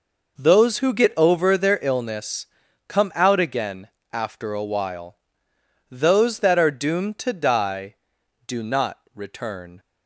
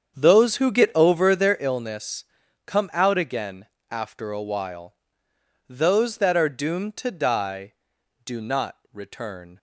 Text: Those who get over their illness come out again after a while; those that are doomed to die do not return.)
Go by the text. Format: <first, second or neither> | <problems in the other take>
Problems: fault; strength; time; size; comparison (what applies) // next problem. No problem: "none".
first | starts louder than the rest; strong; until 1.6 s; 7.5 dB // pauses between "illness" and "come"; at 2.2 s; 0.44 s long; also in the first // pauses between "again" and "after"; slight; at 3.6 s; 0.24 s long; slight in the first // pauses between "not" and "return"; slight; at 8.7 s; 0.16 s long; slight in the first